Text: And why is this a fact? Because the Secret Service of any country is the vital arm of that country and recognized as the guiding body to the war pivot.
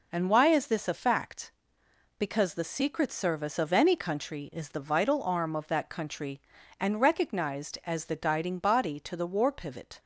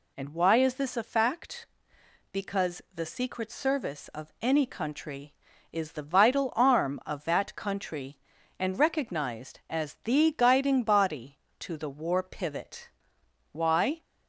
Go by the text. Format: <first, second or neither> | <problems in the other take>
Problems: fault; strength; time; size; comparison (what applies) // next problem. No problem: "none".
first | goes on to say "Why"; from 13.5 s on; 0.50 s long